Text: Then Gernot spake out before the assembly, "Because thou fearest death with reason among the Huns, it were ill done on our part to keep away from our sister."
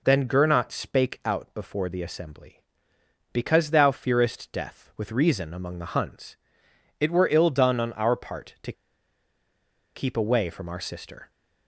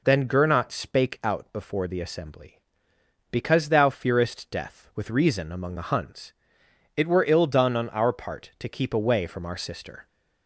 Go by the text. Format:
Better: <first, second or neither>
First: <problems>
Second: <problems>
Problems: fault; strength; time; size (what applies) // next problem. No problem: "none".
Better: second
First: pauses between "to" and "keep"; at 8.7 s; 1.2 s long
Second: none